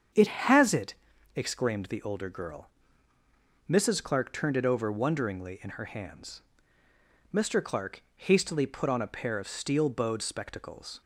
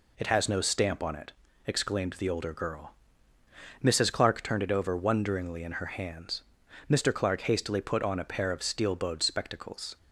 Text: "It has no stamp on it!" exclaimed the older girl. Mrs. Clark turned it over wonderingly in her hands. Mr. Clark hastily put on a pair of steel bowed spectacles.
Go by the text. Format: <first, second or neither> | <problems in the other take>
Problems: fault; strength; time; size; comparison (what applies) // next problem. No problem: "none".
second | starts louder than the rest; strong; until 1.5 s; 7.5 dB // skips "no stamp on"; at 0.7 s